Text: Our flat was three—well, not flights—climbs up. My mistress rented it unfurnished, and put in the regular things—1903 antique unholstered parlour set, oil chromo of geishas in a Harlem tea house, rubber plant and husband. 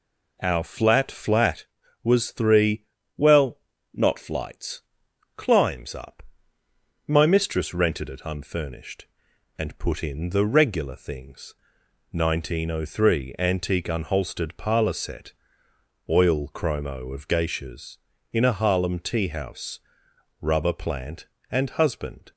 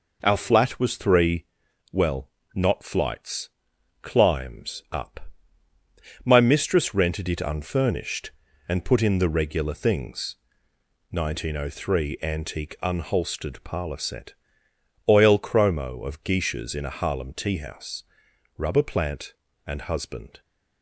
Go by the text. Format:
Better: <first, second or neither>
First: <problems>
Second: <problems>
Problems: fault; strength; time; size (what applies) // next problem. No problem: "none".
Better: second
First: says "flat" twice; at 1.0 s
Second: none